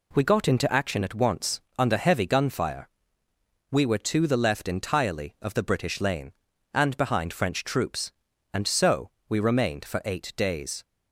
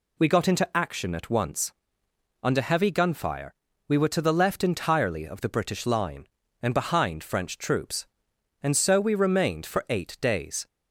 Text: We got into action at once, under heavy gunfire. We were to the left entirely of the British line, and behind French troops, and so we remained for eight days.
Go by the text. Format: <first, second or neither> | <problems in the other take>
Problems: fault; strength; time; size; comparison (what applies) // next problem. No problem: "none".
second | says "lane" for "line"; at 6.0 s // pauses between "so" and "we"; slight; at 9.0 s; 0.20 s long